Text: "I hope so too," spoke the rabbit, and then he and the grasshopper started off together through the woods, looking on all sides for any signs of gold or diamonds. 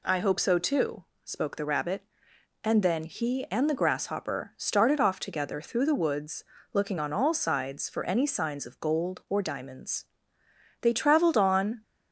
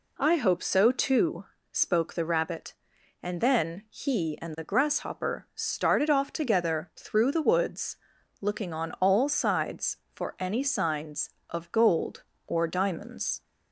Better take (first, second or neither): second